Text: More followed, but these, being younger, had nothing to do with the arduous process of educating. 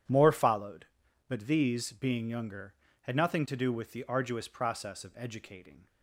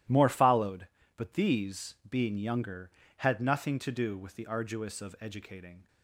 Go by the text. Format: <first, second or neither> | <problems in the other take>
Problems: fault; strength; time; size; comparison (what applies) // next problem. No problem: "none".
first | starts louder than the rest; strong; until 1.3 s; 13.5 dB; strong in the first // skips "process"; at 5.0 s